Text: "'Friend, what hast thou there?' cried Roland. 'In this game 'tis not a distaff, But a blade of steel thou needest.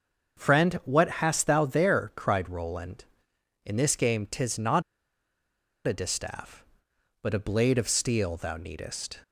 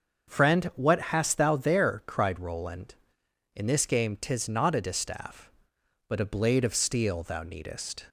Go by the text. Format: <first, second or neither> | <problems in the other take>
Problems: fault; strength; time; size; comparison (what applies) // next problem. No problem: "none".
second | starts louder than the rest; until 1.4 s; 6.5 dB; also in the second // pauses between "not" and "a"; at 4.8 s; 1.0 s long